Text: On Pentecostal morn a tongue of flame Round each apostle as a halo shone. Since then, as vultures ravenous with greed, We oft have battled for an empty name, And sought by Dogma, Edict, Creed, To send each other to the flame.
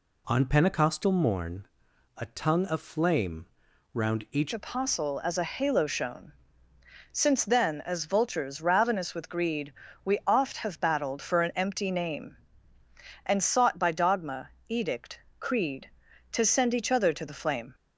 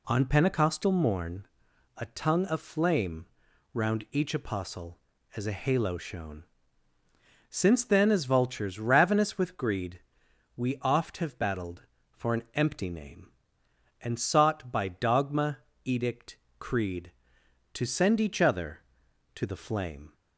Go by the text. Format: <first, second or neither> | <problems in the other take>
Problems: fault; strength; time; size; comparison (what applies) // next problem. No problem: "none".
second | pauses between "morn" and "a"; noticeable; at 1.6 s; 0.50 s long; noticeable in the second // pauses between "flame" and "Round"; noticeable; at 3.4 s; 0.48 s long; noticeable in the second // changes voice at "apostle"; from 4.5 s on; 13.2 s long